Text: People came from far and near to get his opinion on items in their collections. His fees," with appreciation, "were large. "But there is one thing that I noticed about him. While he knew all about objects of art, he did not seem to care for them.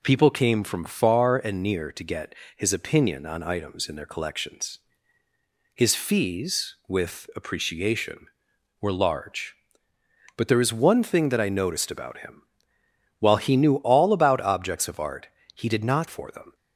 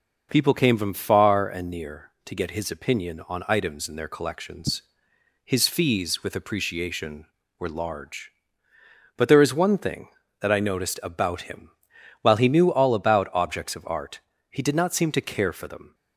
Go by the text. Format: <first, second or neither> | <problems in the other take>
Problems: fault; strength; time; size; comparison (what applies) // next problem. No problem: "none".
second | pauses between "get" and "his"; slight; at 2.3 s; 0.22 s long // skips "seem to care"; at 16.0 s